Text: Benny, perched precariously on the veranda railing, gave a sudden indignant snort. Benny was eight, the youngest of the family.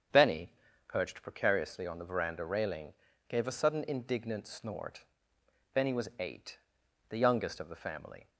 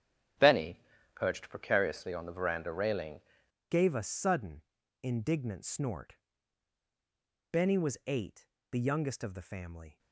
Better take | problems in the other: first | starts louder than the rest; strong; until 1.7 s; 10 dB; strong in the first // changes voice at "gave"; from 3.6 s on; 6.3 s long // pauses between "sudden" and "indignant"; at 4.6 s; 0.40 s long

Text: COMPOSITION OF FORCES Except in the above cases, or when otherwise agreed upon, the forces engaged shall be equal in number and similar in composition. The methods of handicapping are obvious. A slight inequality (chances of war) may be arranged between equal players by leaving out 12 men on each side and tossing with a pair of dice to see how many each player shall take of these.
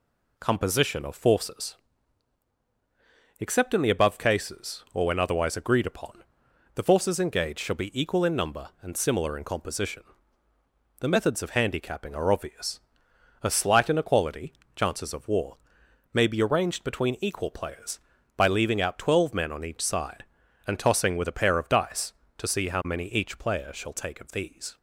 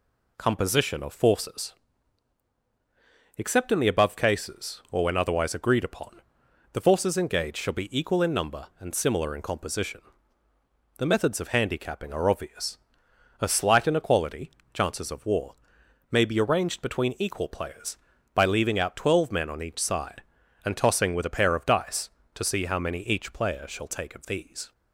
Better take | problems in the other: neither | pauses between "FORCES" and "Except"; strong; the same in both

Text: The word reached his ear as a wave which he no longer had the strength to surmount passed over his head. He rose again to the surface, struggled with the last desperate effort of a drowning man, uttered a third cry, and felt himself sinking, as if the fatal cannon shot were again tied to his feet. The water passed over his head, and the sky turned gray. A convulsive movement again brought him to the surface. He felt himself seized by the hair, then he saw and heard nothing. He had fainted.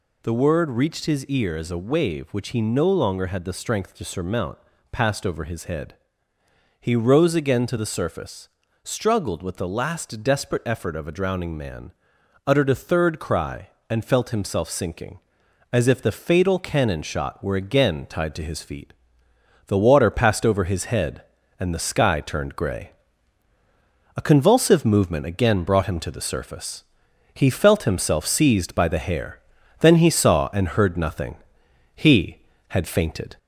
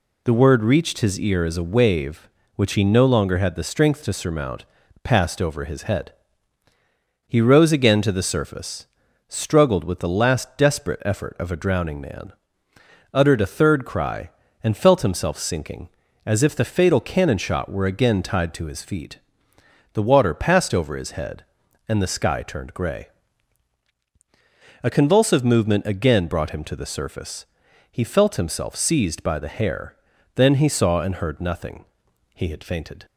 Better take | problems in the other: second | gets louder; slight; throughout; 2 dB // pauses between "surmount" and "passed"; slight; at 4.5 s; 0.34 s long; also in the second

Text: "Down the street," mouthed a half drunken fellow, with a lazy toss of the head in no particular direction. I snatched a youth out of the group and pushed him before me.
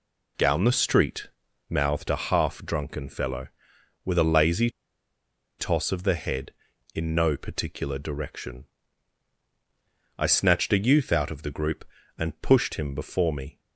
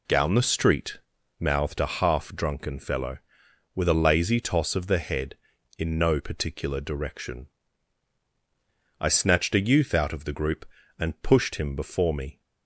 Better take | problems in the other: second | pauses between "lazy" and "toss"; noticeable; at 4.6 s; 0.89 s long

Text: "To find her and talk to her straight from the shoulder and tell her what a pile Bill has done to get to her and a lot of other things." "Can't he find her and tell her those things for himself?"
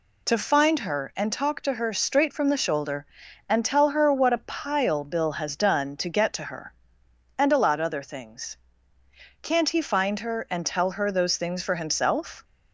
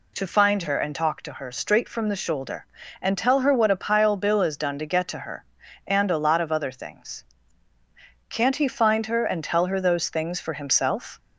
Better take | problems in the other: second | skips "of"; at 7.8 s

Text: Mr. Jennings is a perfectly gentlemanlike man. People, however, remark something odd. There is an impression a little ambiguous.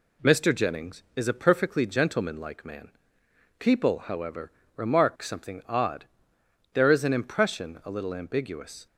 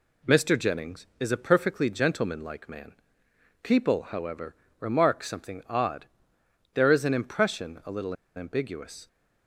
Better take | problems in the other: first | pauses between "little" and "ambiguous"; slight; at 8.1 s; 0.21 s long

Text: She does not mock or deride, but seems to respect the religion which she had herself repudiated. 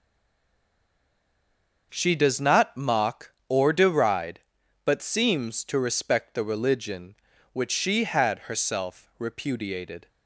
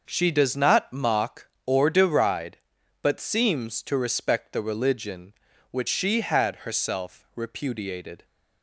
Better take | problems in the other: second | stays silent before the first word; noticeable; until 1.9 s; 1.9 s long // starts louder than the rest; noticeable; until 2.9 s; 6 dB; noticeable in the second

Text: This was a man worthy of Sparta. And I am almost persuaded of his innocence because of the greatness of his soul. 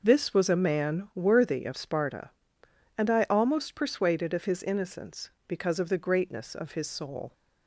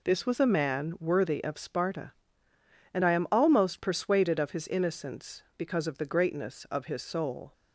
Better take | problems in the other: second | skips "am"; at 3.2 s

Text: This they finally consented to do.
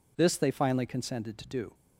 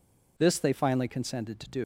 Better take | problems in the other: first | leaves "do" unfinished; at 1.8 s; 115 ms

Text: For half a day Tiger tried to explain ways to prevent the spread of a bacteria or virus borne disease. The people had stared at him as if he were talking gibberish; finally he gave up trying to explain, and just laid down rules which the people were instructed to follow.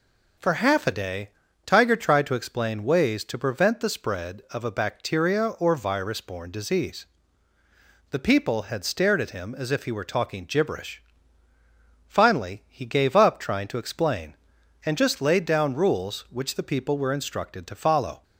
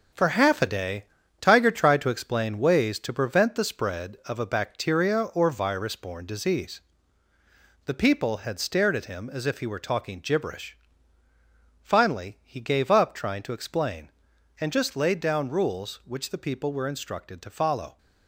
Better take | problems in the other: first | gets quieter; strong; throughout; 7.5 dB // pauses between "day" and "Tiger"; slight; at 1.0 s; 0.34 s long; slight in the first

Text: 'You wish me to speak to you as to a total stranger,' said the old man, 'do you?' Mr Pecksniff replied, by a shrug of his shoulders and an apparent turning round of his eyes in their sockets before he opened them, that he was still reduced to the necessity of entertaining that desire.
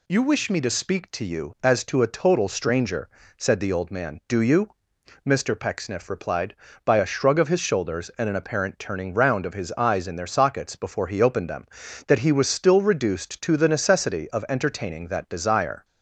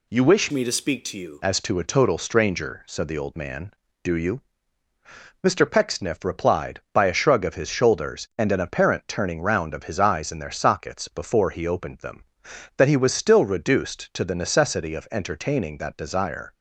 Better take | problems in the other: first | changes voice from "me" to "you"; from 0.5 to 1.4 s; 0.9 s long

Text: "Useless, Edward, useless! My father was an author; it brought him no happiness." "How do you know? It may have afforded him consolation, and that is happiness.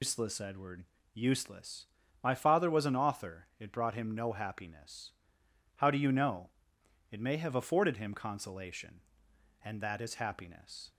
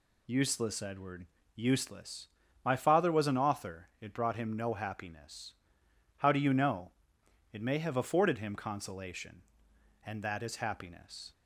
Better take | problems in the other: second | loses the start of "Useless"; at 0.0 s; 170 ms

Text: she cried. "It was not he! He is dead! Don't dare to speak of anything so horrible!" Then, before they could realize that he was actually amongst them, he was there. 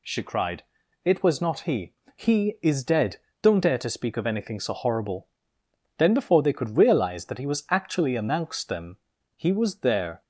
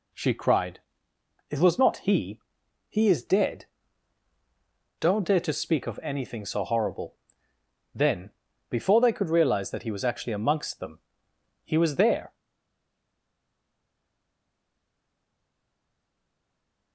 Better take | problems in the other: first | stays silent after the last word; strong; from 12.3 s on; 4.6 s long

